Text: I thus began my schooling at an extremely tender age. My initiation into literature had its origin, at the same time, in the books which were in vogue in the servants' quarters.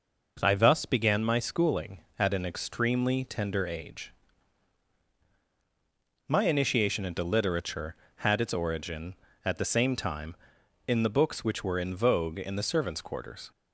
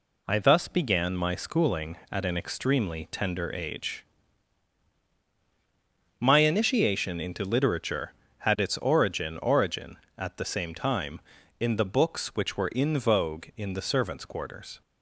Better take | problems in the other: first | says "origin" twice; at 9.3 s

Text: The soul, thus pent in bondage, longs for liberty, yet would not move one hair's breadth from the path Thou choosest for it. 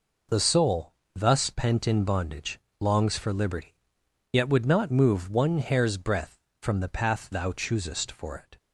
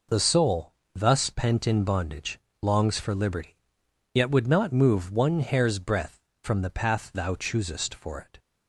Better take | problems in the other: neither | none

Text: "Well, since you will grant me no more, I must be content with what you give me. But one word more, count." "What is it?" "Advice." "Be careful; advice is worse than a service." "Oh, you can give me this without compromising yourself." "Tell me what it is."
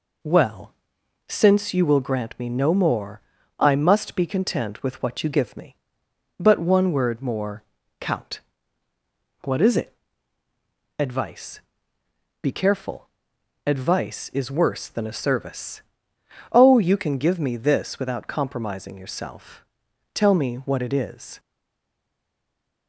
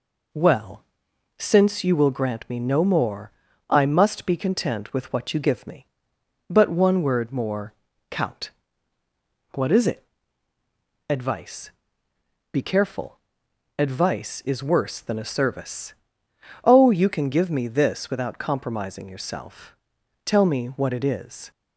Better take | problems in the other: second | stays silent after the last word; noticeable; from 21.3 s on; 1.5 s long

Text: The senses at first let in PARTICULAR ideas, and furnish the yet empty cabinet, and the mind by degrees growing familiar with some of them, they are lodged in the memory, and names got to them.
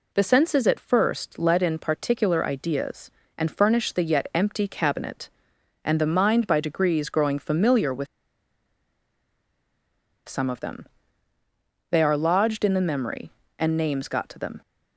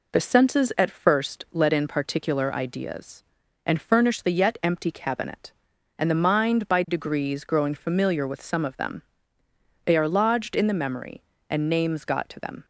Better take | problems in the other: second | pauses between "with" and "some"; strong; at 8.0 s; 2.2 s long

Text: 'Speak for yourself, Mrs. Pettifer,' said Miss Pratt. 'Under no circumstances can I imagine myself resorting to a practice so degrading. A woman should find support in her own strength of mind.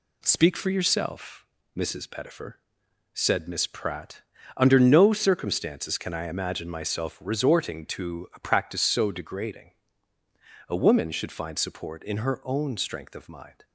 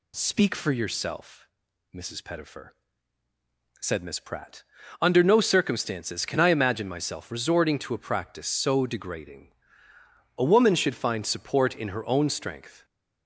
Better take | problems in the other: first | stops before "of mind"; at 12.8 s

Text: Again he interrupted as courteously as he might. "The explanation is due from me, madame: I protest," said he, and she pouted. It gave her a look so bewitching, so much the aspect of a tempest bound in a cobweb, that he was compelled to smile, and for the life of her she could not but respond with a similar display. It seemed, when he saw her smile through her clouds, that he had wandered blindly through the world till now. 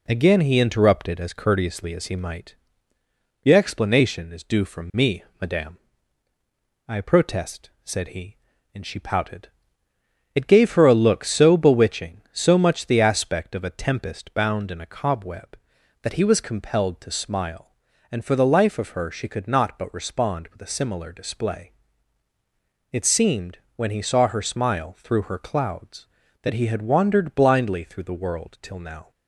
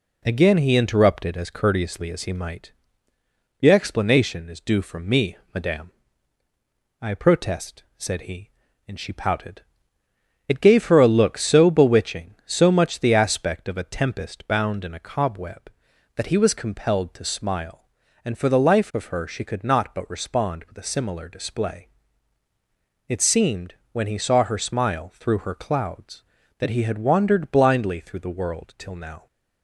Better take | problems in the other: neither | none

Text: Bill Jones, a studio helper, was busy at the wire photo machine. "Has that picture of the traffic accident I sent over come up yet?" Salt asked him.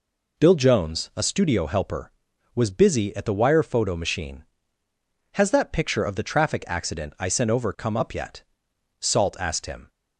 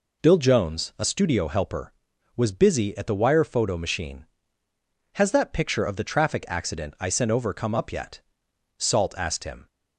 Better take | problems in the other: neither | none

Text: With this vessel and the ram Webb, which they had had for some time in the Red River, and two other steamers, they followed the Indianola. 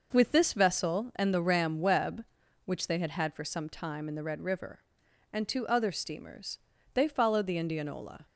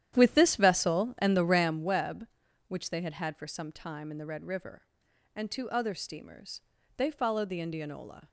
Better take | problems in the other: first | starts louder than the rest; strong; until 1.9 s; 11 dB

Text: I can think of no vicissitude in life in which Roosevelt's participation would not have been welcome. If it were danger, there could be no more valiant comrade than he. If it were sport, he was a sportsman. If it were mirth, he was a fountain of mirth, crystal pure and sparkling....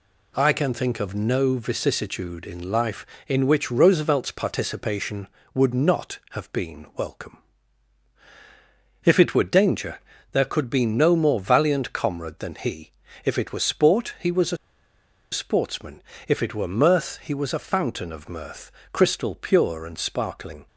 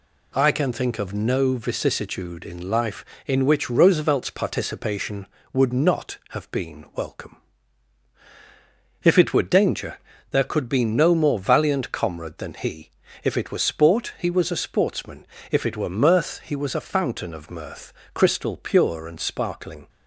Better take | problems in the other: second | pauses between "a" and "sportsman"; noticeable; at 14.5 s; 0.76 s long

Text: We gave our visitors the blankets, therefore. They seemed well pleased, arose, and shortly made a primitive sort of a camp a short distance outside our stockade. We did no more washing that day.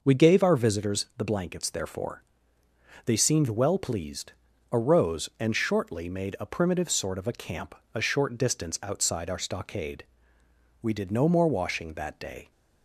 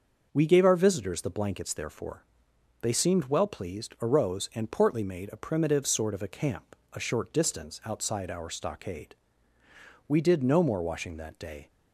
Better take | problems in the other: first | starts louder than the rest; until 1.3 s; 6 dB // says "portly" for "shortly"; at 4.7 s // pauses between "camp" and "a"; slight; at 6.7 s; 0.16 s long; slight in the first

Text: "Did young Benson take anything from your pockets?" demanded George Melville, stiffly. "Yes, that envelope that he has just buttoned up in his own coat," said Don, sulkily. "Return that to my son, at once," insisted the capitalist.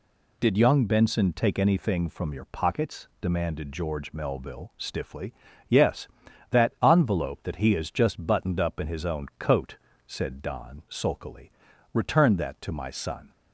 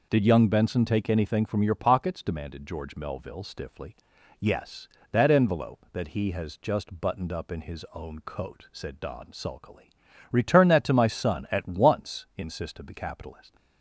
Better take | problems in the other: second | stops before "at once insisted the capitalist"; at 13.3 s

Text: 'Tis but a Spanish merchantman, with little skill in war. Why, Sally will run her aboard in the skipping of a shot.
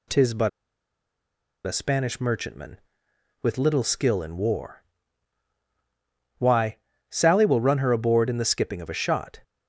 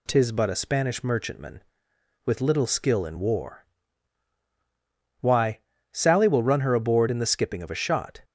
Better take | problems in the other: second | pauses between "but" and "a"; at 0.4 s; 1.1 s long

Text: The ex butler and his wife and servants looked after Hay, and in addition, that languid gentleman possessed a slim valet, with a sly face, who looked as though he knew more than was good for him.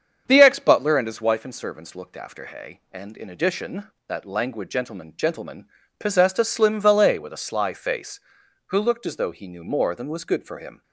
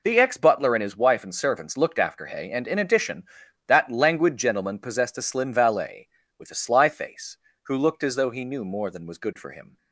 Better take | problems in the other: second | starts louder than the rest; strong; until 1.2 s; 7.5 dB // says "gentleman" twice; at 5.1 s

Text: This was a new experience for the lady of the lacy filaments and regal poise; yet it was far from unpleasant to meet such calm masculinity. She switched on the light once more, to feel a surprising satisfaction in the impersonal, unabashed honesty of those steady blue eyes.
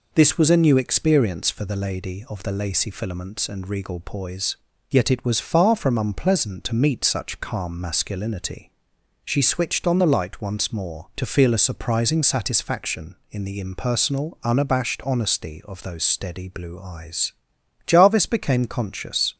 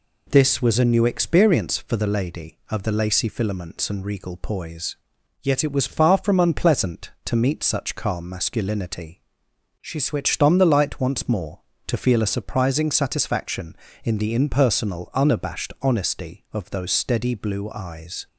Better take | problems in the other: second | goes on to say "Jarvis became conscious"; from 17.8 s on; 1.4 s long

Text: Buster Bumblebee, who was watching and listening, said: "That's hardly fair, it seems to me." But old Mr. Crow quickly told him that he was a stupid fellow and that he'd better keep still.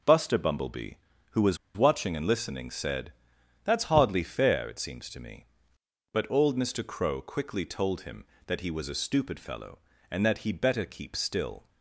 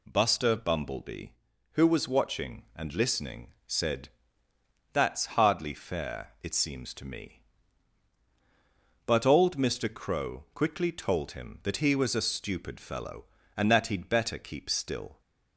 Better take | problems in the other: second | pauses between "was" and "watching"; slight; at 1.5 s; 0.19 s long

